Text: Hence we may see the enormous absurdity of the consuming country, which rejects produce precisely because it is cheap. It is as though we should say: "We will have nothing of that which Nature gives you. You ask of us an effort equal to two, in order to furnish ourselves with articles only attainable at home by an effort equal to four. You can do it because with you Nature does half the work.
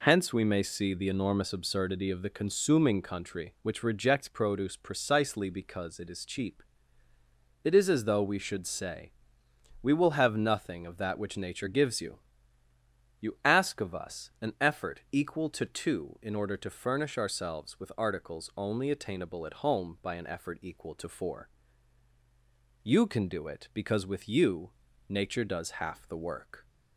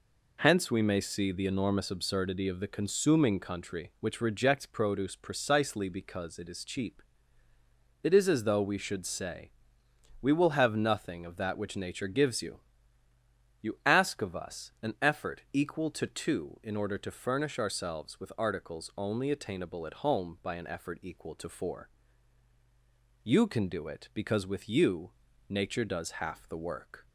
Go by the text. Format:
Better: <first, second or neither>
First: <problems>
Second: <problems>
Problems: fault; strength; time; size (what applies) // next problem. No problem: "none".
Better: neither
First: pauses between "you" and "Nature"; at 24.7 s; 0.38 s long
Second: pauses between "you" and "Nature"; at 25.1 s; 0.38 s long